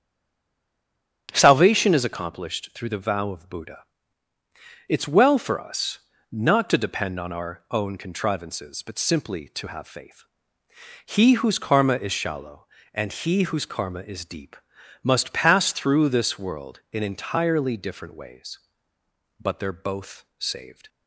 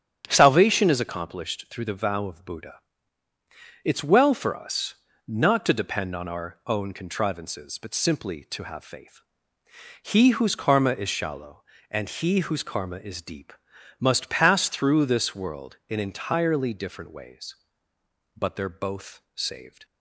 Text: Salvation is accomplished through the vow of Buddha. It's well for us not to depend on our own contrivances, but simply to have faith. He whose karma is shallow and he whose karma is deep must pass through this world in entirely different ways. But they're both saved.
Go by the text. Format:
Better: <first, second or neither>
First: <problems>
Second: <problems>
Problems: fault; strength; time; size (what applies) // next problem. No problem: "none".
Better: second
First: stays silent before the first word; noticeable; until 1.2 s; 1.2 s long // starts louder than the rest; strong; until 2.3 s; 9 dB // pauses between "us" and "not"; slight; at 5.9 s; 0.30 s long // pauses between "deep" and "must"; noticeable; at 14.5 s; 0.46 s long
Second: starts louder than the rest; strong; until 1.2 s; 9 dB // pauses between "us" and "not"; slight; at 4.9 s; 0.30 s long // pauses between "deep" and "must"; noticeable; at 13.5 s; 0.46 s long